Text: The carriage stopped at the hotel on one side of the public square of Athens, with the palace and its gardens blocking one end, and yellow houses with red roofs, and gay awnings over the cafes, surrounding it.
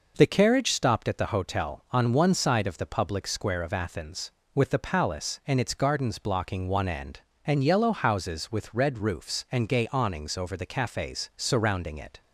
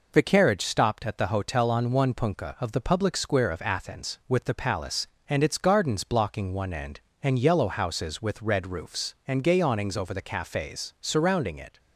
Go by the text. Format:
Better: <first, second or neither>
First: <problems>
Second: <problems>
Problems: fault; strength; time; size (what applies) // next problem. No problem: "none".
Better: first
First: none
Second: says "punka" for "side"; at 2.1 s